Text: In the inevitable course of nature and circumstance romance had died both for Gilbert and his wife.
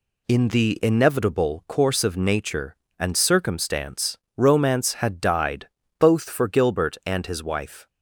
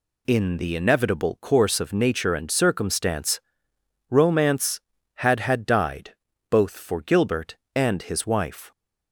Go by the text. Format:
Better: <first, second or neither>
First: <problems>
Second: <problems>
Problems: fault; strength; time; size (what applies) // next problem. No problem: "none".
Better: first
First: pauses between "circumstance" and "romance"; slight; at 4.1 s; 0.22 s long // pauses between "died" and "both"; slight; at 5.6 s; 0.30 s long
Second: pauses between "circumstance" and "romance"; noticeable; at 3.3 s; 0.70 s long // says "had" twice; at 5.4 s // pauses between "died" and "both"; slight; at 6.1 s; 0.36 s long